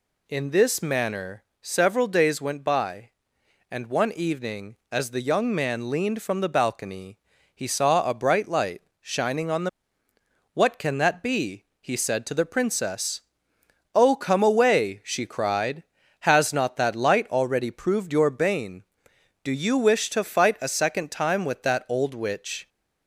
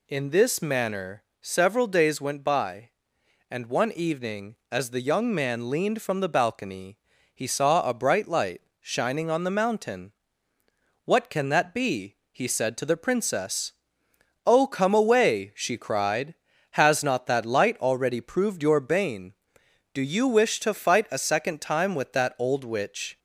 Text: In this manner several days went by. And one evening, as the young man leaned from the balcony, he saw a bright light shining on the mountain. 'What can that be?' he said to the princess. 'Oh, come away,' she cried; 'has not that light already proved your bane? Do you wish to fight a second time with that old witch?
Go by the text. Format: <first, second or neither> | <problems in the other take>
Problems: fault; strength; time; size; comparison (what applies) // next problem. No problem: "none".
second | pauses between "manner" and "several"; slight; at 1.4 s; 0.18 s long; slight in the second // pauses between "light" and "shining"; slight; at 8.8 s; 0.18 s long; slight in the second // skips "mountain"; at 10.1 s